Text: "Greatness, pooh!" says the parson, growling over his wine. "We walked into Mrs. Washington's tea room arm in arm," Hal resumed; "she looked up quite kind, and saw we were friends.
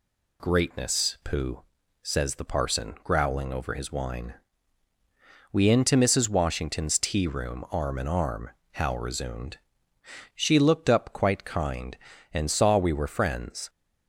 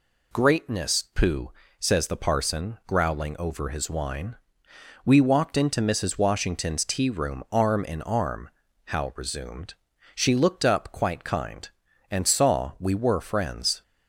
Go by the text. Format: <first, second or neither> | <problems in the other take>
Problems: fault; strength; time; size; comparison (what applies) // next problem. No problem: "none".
second | skips "walked"; at 5.6 s